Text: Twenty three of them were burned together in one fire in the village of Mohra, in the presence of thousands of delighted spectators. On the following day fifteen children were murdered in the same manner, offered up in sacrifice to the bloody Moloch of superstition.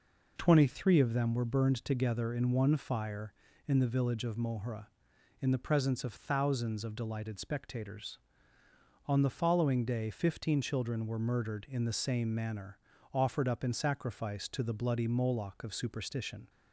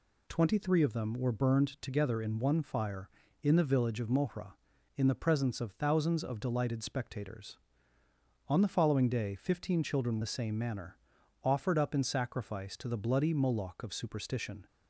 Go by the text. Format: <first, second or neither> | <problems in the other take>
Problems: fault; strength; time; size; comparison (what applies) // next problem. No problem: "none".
first | skips "were murdered in"; at 10.2 s